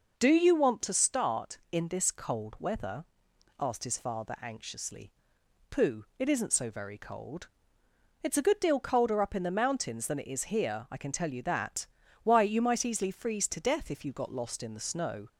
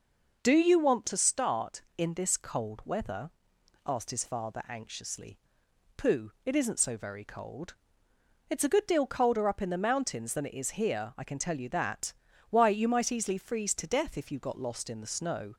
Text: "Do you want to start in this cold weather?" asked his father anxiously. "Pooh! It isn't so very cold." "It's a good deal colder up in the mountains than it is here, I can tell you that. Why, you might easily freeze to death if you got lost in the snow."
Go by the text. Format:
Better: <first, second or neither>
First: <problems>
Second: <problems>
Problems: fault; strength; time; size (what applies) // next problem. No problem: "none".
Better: neither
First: none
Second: none